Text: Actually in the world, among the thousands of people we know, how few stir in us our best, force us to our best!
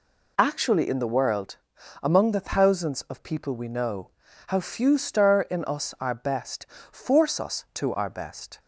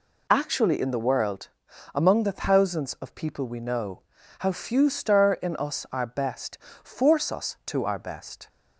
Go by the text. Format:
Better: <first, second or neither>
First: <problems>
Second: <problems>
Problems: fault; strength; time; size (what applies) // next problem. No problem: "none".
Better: neither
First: none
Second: none